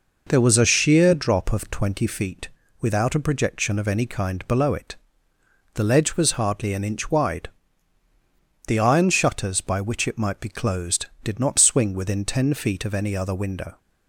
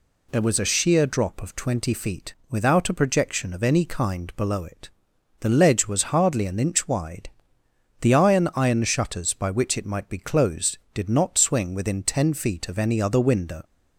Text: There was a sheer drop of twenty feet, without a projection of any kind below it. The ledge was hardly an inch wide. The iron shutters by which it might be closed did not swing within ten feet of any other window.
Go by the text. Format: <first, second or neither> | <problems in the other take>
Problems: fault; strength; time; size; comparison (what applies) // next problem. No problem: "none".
first | says "iron" twice; at 8.5 s